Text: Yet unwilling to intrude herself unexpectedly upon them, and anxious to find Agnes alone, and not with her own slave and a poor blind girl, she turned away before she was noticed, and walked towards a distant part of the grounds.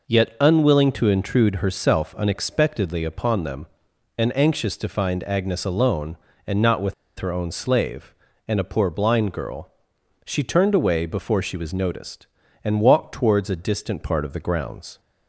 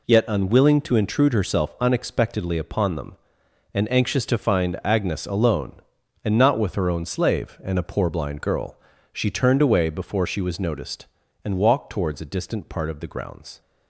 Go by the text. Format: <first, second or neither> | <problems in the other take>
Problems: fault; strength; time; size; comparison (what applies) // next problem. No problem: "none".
second | pauses between "with" and "her"; slight; at 6.9 s; 0.25 s long